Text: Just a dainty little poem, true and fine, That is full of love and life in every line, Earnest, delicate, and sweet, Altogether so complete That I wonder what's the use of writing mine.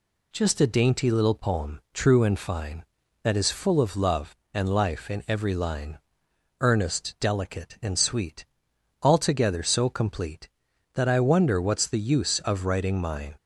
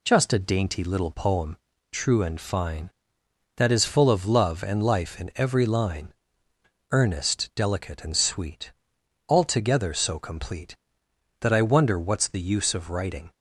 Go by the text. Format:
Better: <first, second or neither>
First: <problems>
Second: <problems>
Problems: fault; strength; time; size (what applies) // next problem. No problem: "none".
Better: first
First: none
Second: stops before "mine"; at 13.3 s